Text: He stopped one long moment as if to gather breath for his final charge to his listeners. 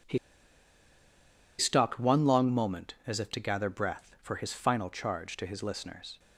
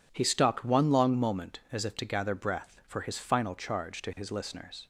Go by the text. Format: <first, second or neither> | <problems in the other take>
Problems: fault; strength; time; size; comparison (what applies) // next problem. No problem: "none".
second | pauses between "He" and "stopped"; strong; at 0.1 s; 1.4 s long